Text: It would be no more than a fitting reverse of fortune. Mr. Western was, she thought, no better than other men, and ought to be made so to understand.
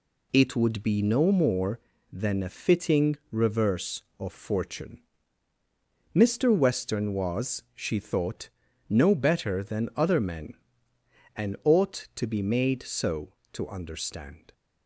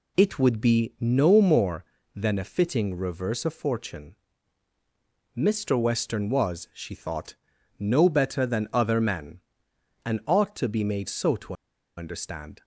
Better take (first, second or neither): first